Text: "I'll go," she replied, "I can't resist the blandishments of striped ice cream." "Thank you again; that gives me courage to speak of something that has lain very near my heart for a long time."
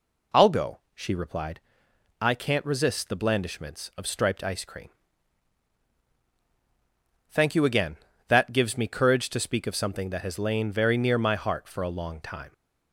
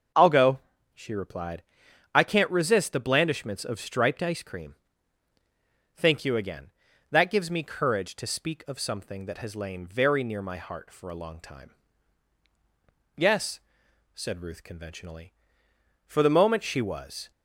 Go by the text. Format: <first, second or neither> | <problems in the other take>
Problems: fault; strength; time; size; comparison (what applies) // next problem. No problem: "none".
first | starts louder than the rest; until 1.4 s; 6.5 dB // goes on to say "Yes said Ruth conventionally For the moment she was"; strong; from 13.1 s on; 4.1 s long